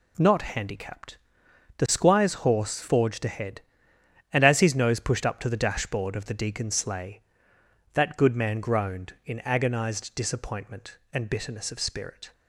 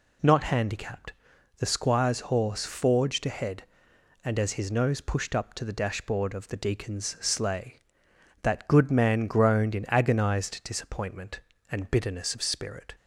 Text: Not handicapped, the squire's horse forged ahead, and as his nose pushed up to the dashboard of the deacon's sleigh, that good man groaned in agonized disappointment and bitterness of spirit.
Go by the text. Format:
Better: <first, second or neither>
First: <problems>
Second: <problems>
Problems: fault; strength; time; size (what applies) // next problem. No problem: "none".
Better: neither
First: none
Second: none